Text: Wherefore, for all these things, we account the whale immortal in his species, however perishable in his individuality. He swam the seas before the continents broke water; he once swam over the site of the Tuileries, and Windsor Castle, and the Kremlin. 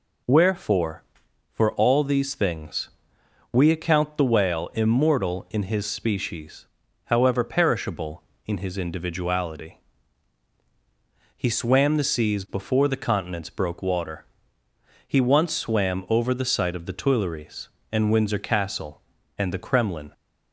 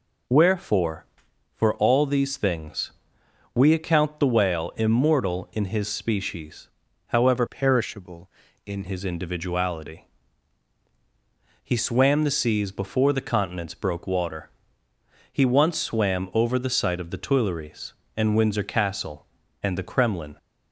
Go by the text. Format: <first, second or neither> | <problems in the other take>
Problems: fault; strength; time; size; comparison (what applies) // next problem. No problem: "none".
first | changes voice from "perishable" to "in"; from 7.4 to 8.8 s; 1.4 s long